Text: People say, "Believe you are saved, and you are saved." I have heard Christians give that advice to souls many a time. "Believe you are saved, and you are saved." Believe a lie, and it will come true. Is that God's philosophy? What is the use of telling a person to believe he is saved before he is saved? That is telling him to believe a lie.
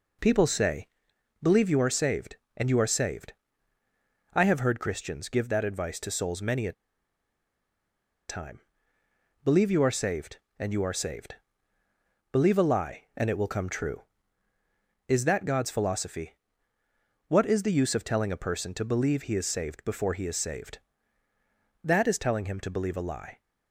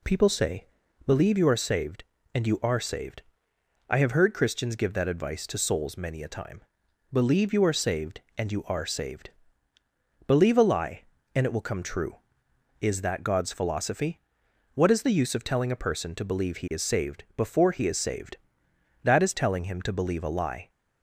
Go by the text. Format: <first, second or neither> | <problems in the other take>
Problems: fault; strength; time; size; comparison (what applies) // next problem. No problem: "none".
second | pauses between "a" and "time"; strong; at 6.7 s; 1.5 s long